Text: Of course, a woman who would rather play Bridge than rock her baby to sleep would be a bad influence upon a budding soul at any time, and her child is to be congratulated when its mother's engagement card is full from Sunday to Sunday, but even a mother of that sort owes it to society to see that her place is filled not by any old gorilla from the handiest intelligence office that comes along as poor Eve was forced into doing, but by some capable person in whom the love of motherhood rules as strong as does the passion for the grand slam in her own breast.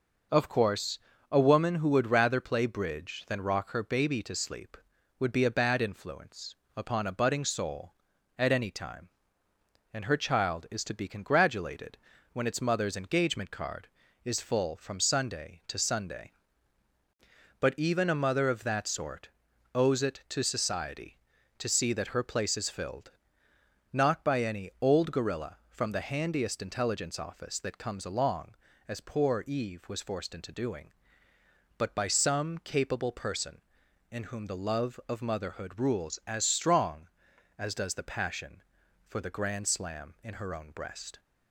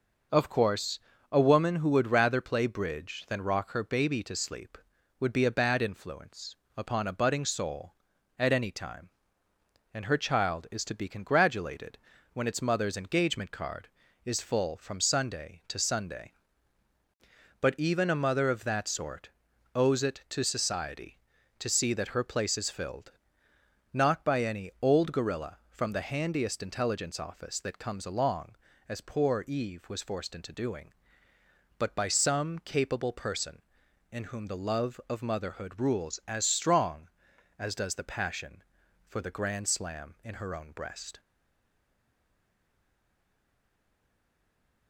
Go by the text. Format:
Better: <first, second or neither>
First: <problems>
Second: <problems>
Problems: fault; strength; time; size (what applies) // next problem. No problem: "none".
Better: first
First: pauses between "influence" and "upon"; slight; at 6.5 s; 0.24 s long // pauses between "congratulated" and "when"; slight; at 11.9 s; 0.34 s long // pauses between "sort" and "owes"; at 19.2 s; 0.44 s long // pauses between "filled" and "not"; noticeable; at 23.1 s; 0.80 s long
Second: pauses between "influence" and "upon"; slight; at 6.5 s; 0.24 s long // pauses between "congratulated" and "when"; slight; at 11.9 s; 0.34 s long // pauses between "sort" and "owes"; at 19.2 s; 0.44 s long // pauses between "filled" and "not"; noticeable; at 23.1 s; 0.80 s long // stays silent after the last word; strong; from 41.1 s on; 3.7 s long